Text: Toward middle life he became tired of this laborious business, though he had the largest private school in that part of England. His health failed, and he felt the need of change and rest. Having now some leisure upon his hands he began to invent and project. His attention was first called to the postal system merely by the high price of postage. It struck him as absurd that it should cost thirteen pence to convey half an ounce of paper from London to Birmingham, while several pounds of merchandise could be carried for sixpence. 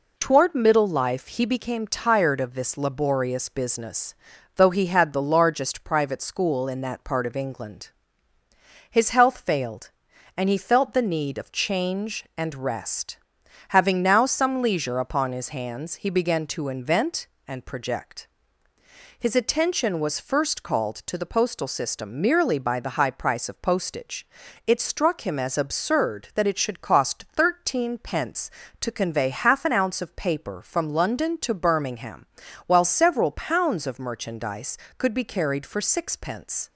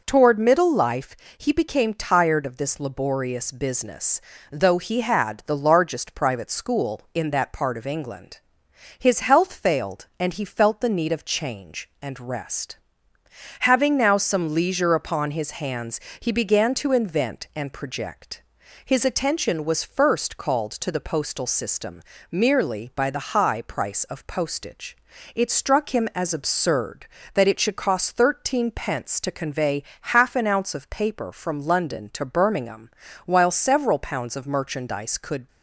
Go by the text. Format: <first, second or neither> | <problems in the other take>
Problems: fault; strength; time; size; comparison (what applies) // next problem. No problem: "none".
first | pauses between "life" and "he"; slight; at 1.1 s; 0.22 s long // pauses between "hands" and "he"; slight; at 15.9 s; 0.20 s long // pauses between "system" and "merely"; slight; at 22.0 s; 0.28 s long // pauses between "convey" and "half"; slight; at 29.8 s; 0.18 s long // stops before "be carried for sixpence"; at 35.4 s